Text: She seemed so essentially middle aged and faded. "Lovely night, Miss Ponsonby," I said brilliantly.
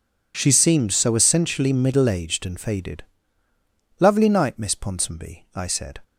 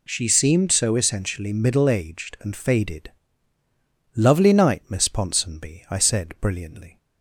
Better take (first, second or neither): second